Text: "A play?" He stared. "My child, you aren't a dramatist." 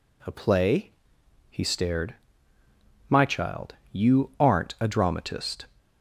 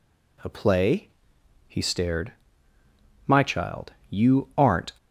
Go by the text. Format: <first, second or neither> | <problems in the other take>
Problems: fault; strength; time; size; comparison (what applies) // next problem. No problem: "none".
first | stops before "a dramatist"; at 4.9 s